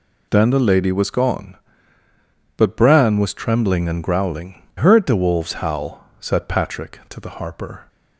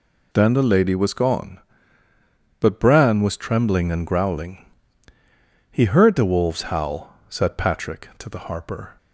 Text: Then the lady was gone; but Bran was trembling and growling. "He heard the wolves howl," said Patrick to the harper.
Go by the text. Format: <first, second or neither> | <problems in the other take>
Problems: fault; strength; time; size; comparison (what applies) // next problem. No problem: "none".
second | skips "He"; at 4.6 s